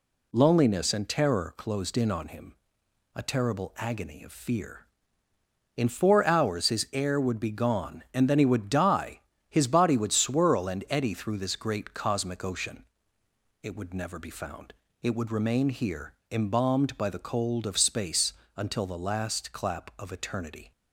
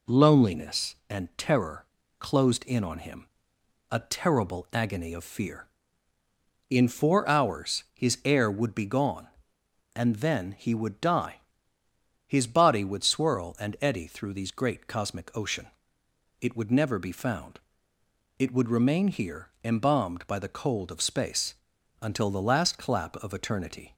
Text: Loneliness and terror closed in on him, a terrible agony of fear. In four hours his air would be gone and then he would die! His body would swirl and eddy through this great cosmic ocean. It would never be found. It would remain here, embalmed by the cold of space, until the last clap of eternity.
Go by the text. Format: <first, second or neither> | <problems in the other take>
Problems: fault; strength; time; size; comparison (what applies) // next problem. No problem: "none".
first | pauses between "terror" and "closed"; slight; at 1.8 s; 0.32 s long // says "these" for "this"; at 14.3 s